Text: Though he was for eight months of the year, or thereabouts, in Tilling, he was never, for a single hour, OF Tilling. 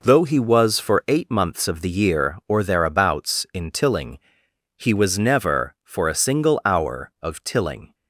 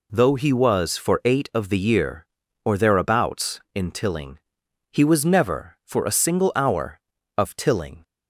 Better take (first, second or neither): first